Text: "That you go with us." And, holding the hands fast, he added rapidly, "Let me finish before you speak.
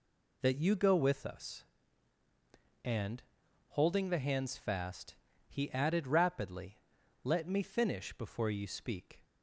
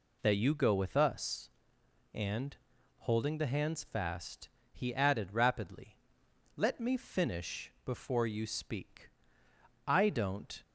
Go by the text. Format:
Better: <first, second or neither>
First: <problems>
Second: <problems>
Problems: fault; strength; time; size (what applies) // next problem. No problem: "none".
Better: first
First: none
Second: goes on to say "I don't"; noticeable; from 9.8 s on; 0.74 s long